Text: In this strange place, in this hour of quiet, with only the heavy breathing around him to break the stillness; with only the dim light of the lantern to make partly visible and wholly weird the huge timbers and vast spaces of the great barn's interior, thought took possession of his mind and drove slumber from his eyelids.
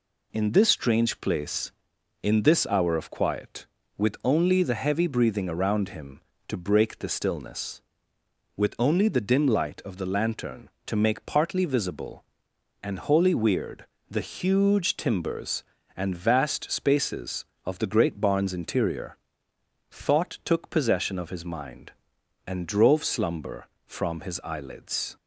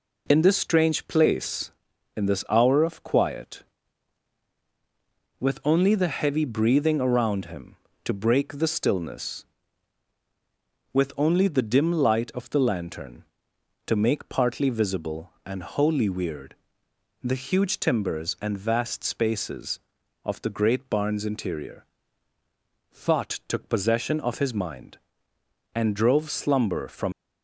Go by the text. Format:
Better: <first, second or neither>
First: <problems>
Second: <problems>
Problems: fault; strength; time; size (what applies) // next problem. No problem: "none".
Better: first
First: pauses between "weird" and "the"; slight; at 13.8 s; 0.24 s long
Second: pauses between "weird" and "the"; noticeable; at 16.5 s; 0.68 s long // stops before "his eyelids"; at 27.1 s